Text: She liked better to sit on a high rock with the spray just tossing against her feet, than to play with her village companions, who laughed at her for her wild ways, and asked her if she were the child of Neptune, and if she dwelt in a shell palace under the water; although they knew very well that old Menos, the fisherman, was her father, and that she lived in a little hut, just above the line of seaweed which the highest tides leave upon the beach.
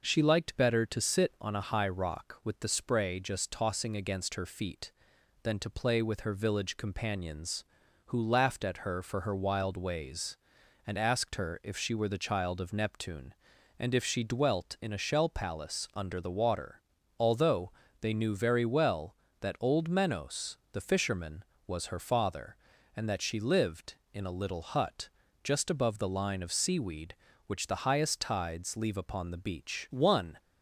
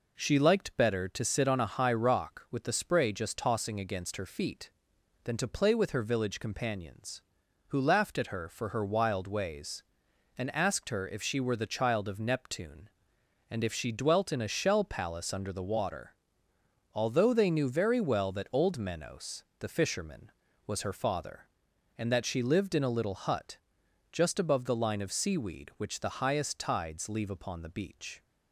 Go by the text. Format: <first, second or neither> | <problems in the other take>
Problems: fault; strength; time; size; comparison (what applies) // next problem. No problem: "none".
second | pauses between "although" and "they"; slight; at 17.7 s; 0.30 s long // goes on to say "One"; slight; from 29.8 s on; 0.48 s long